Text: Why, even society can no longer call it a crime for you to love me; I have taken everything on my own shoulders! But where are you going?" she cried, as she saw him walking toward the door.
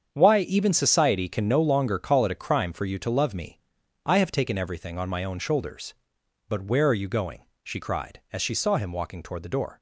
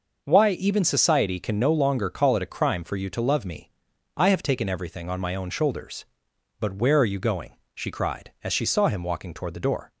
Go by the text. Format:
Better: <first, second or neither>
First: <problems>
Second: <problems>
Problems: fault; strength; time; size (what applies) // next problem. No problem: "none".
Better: second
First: gets quieter; strong; throughout; 10 dB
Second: none